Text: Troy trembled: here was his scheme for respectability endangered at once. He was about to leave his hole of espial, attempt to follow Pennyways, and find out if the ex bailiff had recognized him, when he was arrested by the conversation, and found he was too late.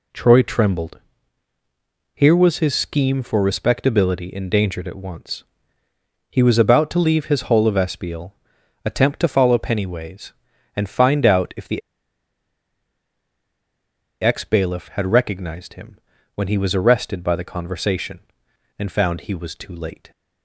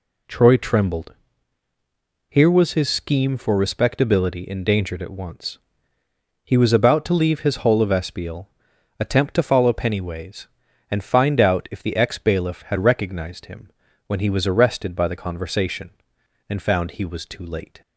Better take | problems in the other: second | pauses between "the" and "ex"; strong; at 11.8 s; 2.4 s long

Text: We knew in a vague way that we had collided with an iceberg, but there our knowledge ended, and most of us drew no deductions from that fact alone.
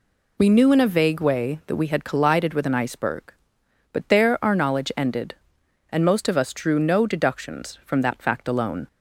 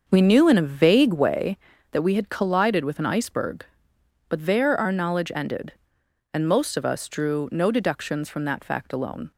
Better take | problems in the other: first | starts louder than the rest; until 1.5 s; 6.5 dB

